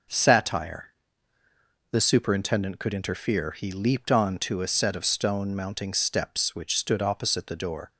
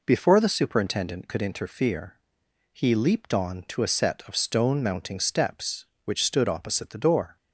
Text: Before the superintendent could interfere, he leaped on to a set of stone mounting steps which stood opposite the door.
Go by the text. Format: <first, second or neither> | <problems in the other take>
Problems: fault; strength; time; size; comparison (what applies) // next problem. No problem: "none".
second | starts louder than the rest; noticeable; until 2.1 s; 6 dB // says "Satire" for "Before"; at 0.1 s